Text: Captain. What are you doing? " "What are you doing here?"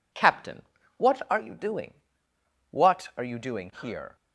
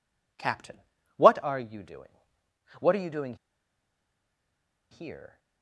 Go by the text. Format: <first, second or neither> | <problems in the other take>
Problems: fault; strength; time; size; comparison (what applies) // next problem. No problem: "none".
first | pauses between "doing" and "here"; strong; at 3.3 s; 1.5 s long